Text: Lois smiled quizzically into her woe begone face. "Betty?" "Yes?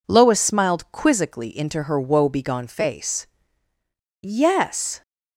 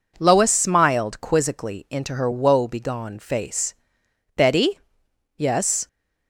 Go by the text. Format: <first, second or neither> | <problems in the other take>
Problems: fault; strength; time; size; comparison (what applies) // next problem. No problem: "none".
second | skips "Betty"; at 3.7 s